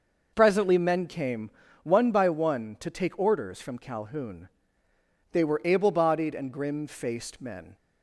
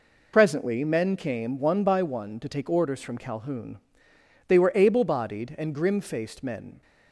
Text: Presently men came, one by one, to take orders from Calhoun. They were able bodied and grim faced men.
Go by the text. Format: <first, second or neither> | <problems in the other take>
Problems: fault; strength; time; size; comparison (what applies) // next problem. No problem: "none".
first | loses the start of "Presently"; at 0.3 s; 40 ms